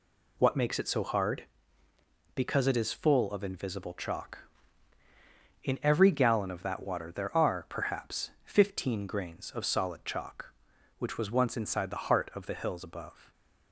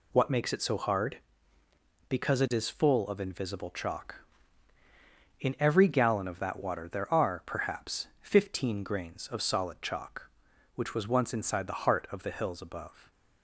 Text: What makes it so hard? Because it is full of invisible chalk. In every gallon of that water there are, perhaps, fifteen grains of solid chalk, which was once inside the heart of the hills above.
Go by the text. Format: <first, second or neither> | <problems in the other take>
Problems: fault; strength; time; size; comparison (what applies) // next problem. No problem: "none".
neither | none